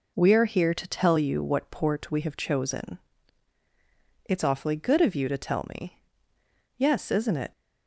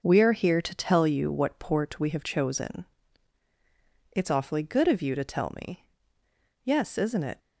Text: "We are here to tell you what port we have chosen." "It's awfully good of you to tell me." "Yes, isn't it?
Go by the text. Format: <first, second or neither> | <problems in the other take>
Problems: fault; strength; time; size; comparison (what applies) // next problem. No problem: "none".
first | gets quieter; strong; throughout; 8 dB